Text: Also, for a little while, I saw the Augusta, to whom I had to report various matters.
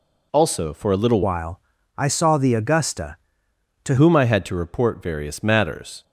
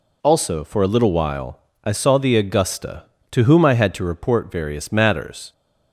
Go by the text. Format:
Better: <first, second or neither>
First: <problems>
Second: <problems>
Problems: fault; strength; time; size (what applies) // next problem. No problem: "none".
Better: second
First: changes voice from "while" to "to"; from 1.2 to 3.9 s; 2.7 s long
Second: none